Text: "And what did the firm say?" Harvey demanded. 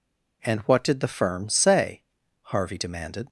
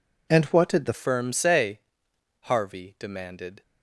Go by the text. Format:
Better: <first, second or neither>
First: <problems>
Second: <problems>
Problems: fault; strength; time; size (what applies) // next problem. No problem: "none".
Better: first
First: none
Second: changes voice at "firm"; from 0.9 s on; 2.7 s long